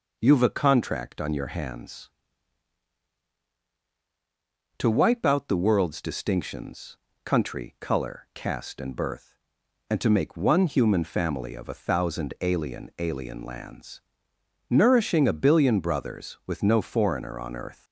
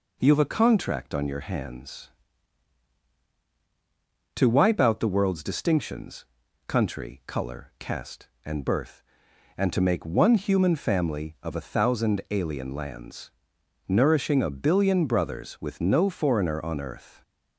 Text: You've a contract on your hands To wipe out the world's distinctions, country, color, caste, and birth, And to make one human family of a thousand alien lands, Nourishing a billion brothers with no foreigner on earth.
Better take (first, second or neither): second